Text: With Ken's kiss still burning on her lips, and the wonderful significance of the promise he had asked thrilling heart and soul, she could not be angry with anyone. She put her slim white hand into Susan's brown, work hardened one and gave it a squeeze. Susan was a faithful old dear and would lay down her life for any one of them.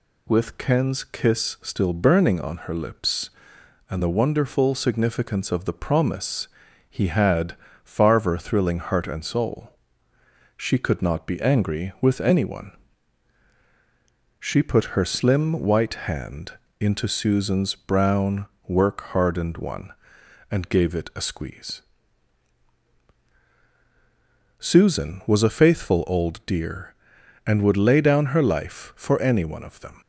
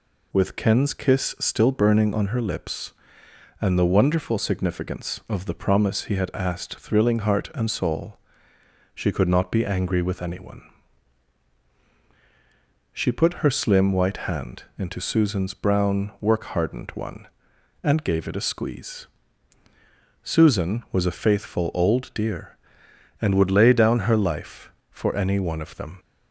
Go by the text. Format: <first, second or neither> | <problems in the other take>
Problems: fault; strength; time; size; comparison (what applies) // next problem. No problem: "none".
second | pauses between "promise" and "he"; at 6.4 s; 0.42 s long // says "farver" for "asked"; at 7.8 s // pauses between "hand" and "into"; slight; at 16.5 s; 0.26 s long